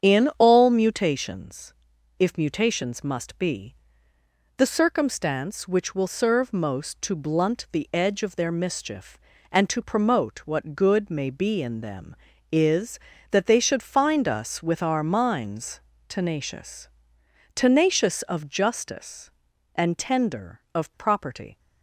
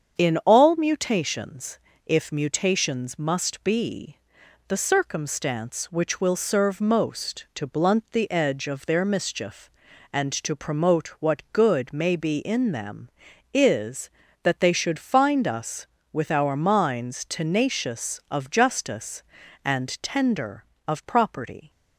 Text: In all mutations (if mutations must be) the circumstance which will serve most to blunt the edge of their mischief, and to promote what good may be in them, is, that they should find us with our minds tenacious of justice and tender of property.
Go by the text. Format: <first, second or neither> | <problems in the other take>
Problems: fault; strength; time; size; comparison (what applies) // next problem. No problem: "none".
second | starts louder than the rest; strong; until 1.0 s; 8 dB; strong in the second // pauses between "minds" and "tenacious"; slight; at 15.8 s; 0.28 s long // says "tenacious" twice; at 17.5 s